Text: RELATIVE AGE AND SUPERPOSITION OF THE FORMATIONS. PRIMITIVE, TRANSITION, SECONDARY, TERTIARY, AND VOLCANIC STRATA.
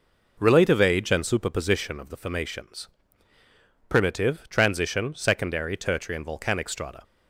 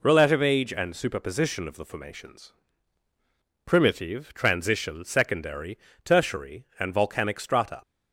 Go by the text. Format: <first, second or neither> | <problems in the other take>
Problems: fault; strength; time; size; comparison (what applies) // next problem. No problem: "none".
neither | none